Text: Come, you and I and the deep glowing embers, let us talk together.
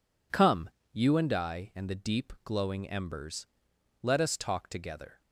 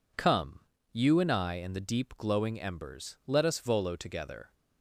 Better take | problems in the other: first | says "volo" for "talk"; at 3.5 s

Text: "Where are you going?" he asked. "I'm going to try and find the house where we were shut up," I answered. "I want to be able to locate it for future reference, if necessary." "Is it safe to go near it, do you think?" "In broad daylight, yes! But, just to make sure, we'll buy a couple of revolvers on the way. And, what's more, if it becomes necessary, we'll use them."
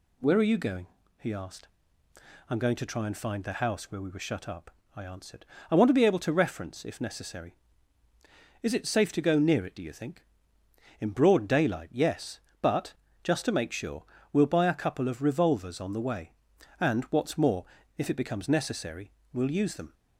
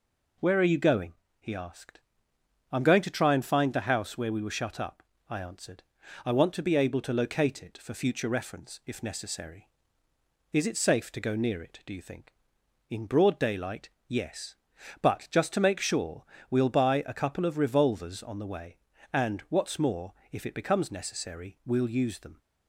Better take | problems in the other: second | skips "locate it for future"; at 6.3 s

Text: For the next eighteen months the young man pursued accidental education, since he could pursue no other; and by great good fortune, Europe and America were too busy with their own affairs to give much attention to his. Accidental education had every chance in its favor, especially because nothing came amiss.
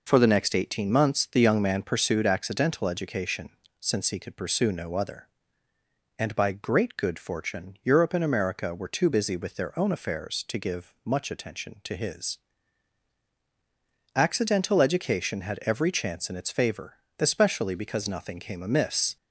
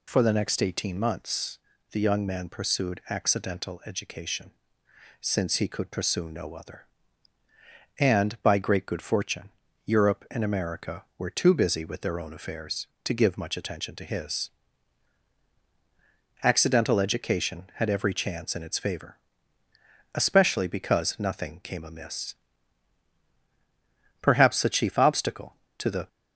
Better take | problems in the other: first | pauses between "months" and "the"; slight; at 1.5 s; 0.32 s long // goes on to say "Perhaps the chief obstacle to the"; strong; from 24.2 s on; 1.8 s long

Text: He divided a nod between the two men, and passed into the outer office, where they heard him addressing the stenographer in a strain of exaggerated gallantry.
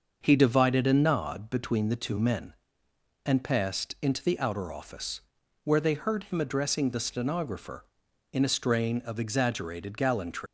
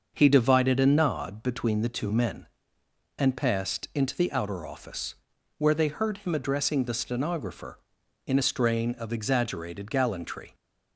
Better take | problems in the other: second | starts louder than the rest; until 1.2 s; 6.5 dB; also in the second // leaves "gallantry" unfinished; at 10.4 s; 145 ms

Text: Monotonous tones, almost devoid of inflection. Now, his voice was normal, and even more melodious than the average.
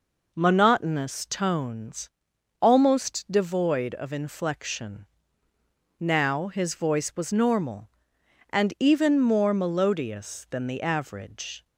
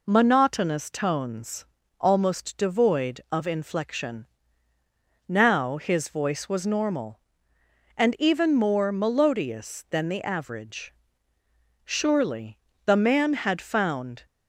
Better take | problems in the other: first | goes on to say "Surely the man had found"; strong; from 11.8 s on; 2.4 s long

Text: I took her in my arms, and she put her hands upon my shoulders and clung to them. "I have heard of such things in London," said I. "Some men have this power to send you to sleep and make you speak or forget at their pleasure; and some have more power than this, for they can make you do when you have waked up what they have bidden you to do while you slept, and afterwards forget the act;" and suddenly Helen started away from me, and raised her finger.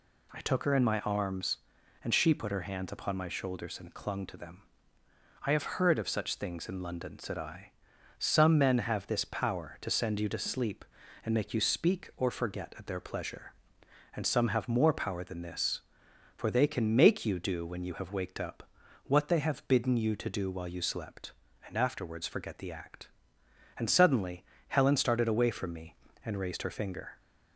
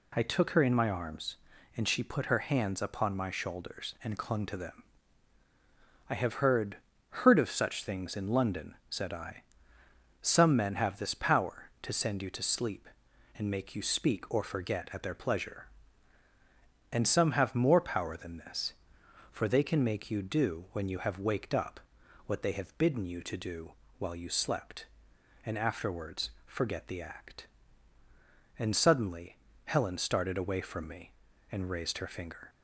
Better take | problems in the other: first | says "heard" twice; at 7.1 s // pauses between "up" and "what"; noticeable; at 21.7 s; 0.46 s long; also in the first // pauses between "do" and "while"; slight; at 23.7 s; 0.26 s long // pauses between "suddenly" and "Helen"; slight; at 29.3 s; 0.28 s long; slight in the first

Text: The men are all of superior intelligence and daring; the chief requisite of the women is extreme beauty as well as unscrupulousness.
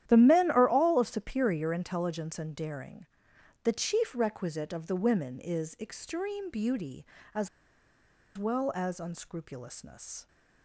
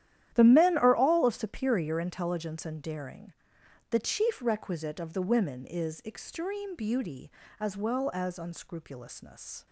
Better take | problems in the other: second | starts louder than the rest; strong; until 1.0 s; 11.5 dB; strong in the second // pauses between "as" and "well"; noticeable; at 7.4 s; 0.88 s long

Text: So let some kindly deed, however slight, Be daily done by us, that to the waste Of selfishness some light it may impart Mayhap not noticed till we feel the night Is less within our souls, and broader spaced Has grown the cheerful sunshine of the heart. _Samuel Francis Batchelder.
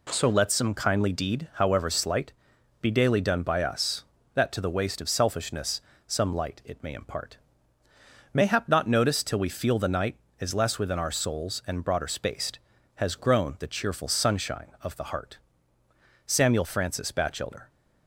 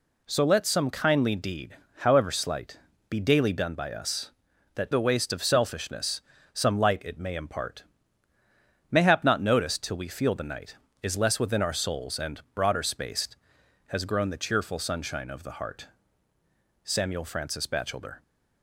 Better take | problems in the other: first | skips "to"; at 4.9 s // pauses between "selfishness" and "some"; slight; at 6.2 s; 0.32 s long; slight in the first // pauses between "impart" and "Mayhap"; at 7.8 s; 1.0 s long; noticeable in the first

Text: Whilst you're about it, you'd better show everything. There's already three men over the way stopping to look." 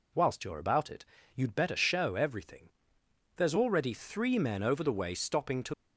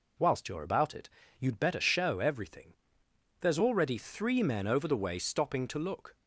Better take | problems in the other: second | stops before "look"; at 5.7 s

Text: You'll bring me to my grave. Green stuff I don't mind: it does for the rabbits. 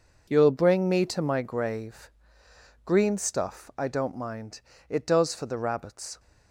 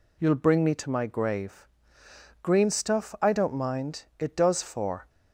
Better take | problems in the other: first | stops before "the rabbits"; at 5.0 s

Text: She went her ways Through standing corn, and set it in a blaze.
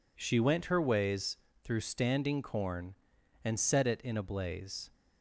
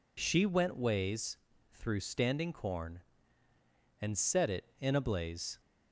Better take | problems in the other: first | skips "her"; at 0.7 s // pauses between "ways" and "Through"; slight; at 1.3 s; 0.36 s long; slight in the first

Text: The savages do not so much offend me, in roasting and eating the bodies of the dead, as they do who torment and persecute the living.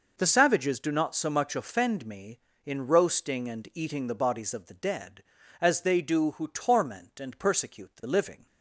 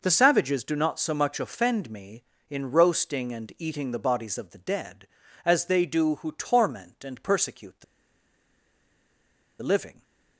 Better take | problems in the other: first | pauses between "the" and "living"; strong; at 7.8 s; 1.7 s long

